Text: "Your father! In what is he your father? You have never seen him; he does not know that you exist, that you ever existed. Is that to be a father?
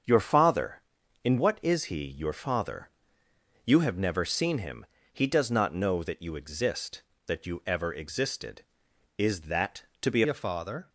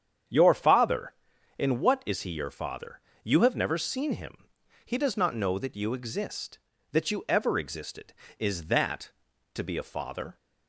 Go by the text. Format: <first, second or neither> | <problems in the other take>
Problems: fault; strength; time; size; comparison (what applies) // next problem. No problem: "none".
second | starts louder than the rest; strong; until 1.5 s; 7 dB; strong in the second // changes voice at "a"; from 10.2 s on; 0.6 s long